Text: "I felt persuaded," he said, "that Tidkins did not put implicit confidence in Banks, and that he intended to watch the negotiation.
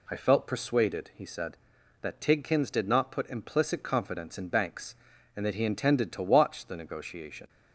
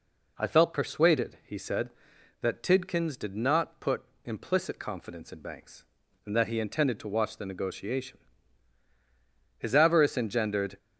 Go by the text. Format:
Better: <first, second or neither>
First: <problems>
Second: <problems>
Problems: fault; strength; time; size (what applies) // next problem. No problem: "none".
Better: first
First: none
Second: pauses between "put" and "implicit"; slight; at 4.0 s; 0.22 s long // goes on to say "His avarice engendered"; noticeable; from 9.5 s on; 1.2 s long